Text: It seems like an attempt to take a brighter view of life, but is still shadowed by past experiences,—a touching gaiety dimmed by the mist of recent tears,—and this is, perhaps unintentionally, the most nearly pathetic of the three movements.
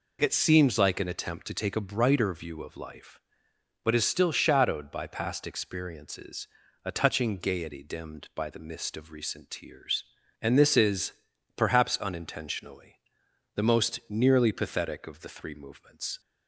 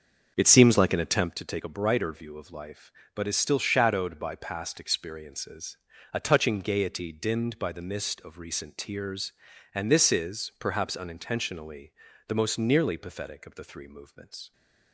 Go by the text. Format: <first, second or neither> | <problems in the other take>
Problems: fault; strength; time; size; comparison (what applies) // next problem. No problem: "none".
first | starts louder than the rest; until 1.3 s; 6.5 dB